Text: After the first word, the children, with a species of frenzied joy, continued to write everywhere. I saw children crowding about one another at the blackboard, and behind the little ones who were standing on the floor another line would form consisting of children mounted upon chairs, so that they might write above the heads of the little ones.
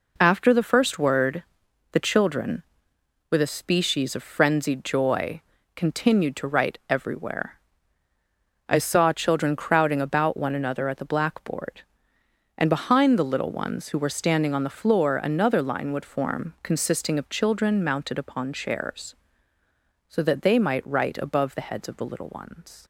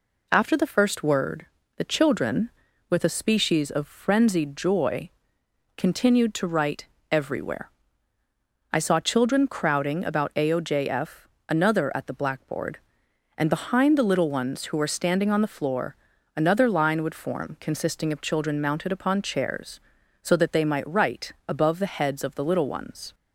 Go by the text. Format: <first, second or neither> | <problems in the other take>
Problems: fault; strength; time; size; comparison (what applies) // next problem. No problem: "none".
first | pauses between "write" and "everywhere"; slight; at 6.8 s; 0.24 s long // says "aojf" for "one"; at 10.3 s // pauses between "floor" and "another"; at 15.9 s; 0.40 s long // pauses between "write" and "above"; slight; at 21.3 s; 0.16 s long